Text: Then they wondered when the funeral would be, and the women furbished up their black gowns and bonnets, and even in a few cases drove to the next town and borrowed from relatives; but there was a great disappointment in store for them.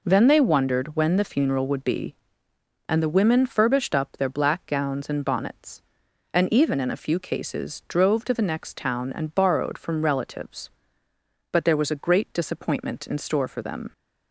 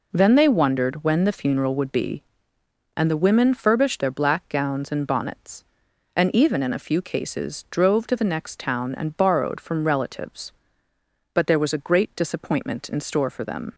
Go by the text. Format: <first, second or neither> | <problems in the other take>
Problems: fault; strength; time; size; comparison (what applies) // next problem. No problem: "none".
first | skips "up"; at 4.0 s